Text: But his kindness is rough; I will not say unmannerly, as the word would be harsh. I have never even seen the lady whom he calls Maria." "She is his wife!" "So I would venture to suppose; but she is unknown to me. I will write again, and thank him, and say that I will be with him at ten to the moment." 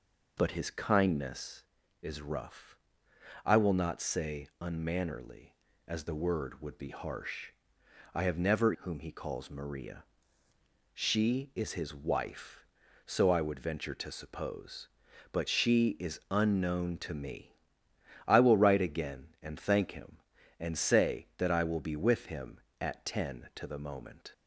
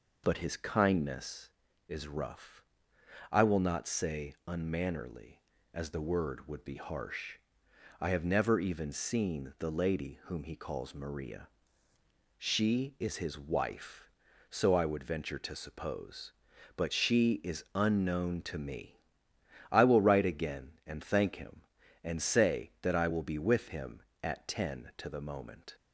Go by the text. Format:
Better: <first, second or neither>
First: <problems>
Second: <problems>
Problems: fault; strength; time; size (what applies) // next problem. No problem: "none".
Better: second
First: skips "even seen the lady"; at 8.7 s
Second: none